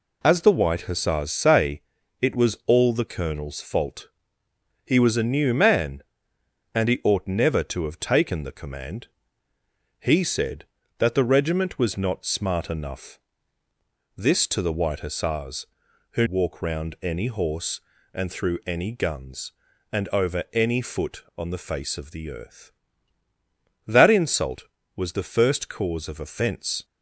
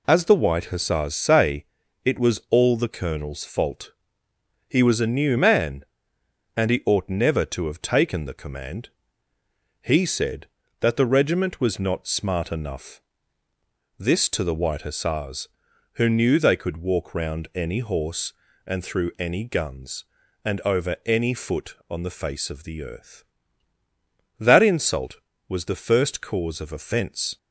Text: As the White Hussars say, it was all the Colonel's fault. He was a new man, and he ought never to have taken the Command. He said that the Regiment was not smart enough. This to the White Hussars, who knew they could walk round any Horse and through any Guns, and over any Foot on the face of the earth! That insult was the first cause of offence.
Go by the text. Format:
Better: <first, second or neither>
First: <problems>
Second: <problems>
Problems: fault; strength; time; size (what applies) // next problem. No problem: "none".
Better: second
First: skips "knew they could"; at 16.2 s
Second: none